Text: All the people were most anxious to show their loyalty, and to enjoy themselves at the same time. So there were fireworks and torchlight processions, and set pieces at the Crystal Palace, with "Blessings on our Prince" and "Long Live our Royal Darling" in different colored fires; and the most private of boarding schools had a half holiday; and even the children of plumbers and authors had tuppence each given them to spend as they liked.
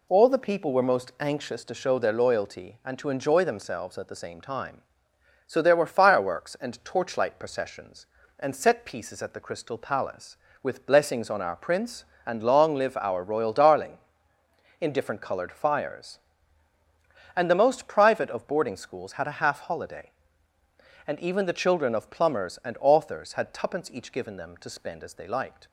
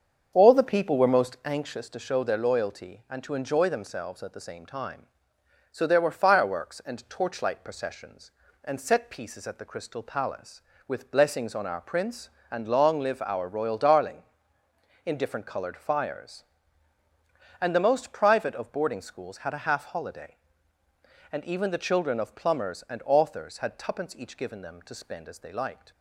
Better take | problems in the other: first | starts louder than the rest; until 1.4 s; 7 dB

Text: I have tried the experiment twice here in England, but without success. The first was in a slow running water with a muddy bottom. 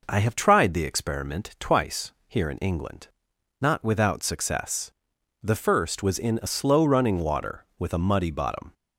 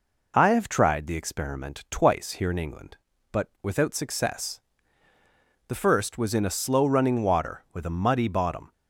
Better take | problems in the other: second | pauses between "twice" and "here"; slight; at 2.1 s; 0.16 s long // says "not" for "but"; at 3.6 s

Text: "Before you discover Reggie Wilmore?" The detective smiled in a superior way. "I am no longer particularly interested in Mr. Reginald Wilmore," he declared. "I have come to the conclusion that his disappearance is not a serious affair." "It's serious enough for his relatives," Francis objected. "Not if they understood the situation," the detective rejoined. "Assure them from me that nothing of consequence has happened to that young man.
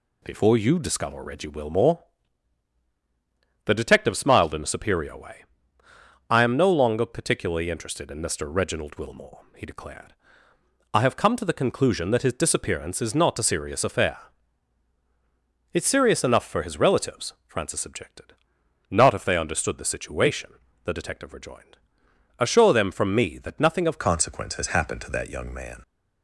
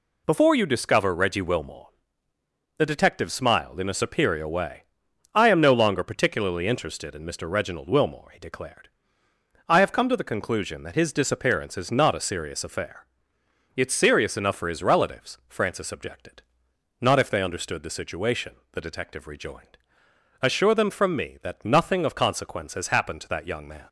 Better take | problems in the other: second | changes voice at "consequence"; from 23.9 s on; 1.9 s long

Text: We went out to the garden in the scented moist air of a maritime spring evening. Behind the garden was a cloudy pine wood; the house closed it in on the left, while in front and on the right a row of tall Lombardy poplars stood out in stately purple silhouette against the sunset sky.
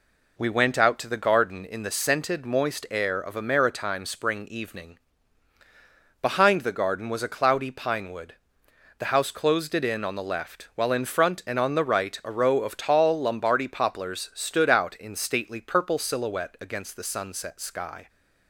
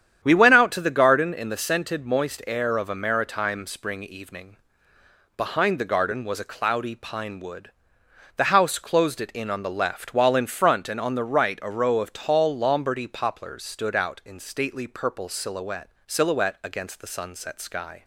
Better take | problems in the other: first | starts louder than the rest; strong; until 1.2 s; 9.5 dB // says "silhouette" twice; at 16.0 s

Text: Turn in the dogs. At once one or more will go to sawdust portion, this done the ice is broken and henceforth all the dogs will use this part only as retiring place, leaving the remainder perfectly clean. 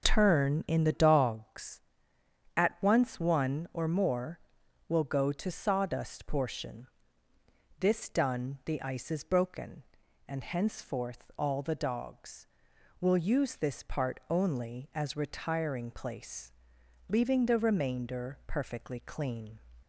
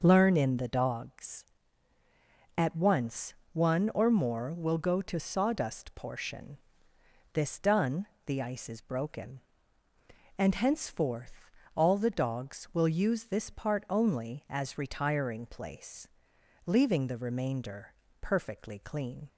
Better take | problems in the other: first | says "Learn" for "Turn"; at 0.0 s // pauses between "once" and "one"; slight; at 3.3 s; 0.20 s long // pauses between "done" and "the"; slight; at 8.0 s; 0.20 s long // pauses between "henceforth" and "all"; slight; at 11.5 s; 0.24 s long // pauses between "remainder" and "perfectly"; slight; at 17.9 s; 0.30 s long

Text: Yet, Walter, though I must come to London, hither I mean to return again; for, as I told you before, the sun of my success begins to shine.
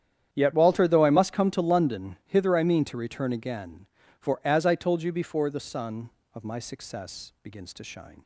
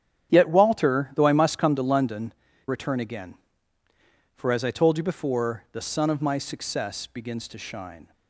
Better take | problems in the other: first | starts louder than the rest; strong; until 1.3 s; 9.5 dB; strong in the first // skips "hither I mean to"; at 2.5 s

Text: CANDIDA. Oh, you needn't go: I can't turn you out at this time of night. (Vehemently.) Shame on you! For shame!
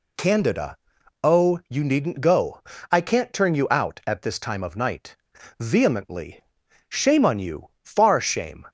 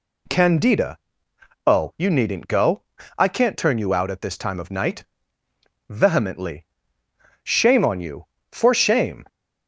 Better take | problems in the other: second | says "Far" for "For"; at 7.8 s

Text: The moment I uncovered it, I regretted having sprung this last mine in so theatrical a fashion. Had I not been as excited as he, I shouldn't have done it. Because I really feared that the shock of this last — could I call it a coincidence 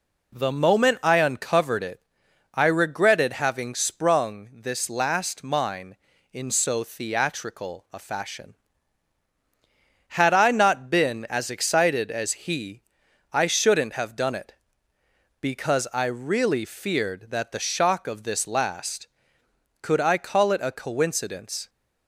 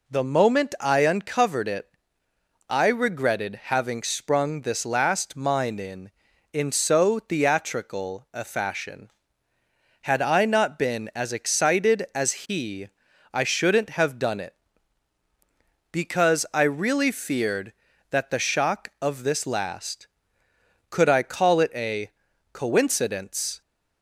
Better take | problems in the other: first | says "in" twice; at 6.5 s // pauses between "a" and "coincidence"; at 22.0 s; 0.44 s long

